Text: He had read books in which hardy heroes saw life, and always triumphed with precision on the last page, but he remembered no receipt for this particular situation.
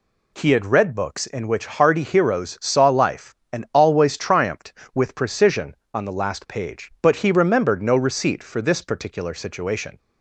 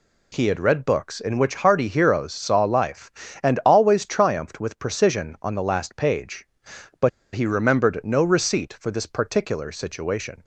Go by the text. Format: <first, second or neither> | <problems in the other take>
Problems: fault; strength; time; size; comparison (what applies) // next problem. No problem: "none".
first | pauses between "but" and "he"; slight; at 7.0 s; 0.24 s long